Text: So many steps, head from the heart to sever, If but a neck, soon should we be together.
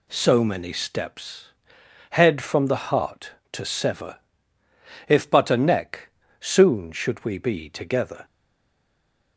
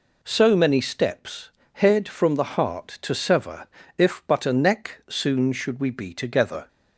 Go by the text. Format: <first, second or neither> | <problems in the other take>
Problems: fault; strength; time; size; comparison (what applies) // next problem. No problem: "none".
second | stays silent after the last word; from 8.2 s on; 1.1 s long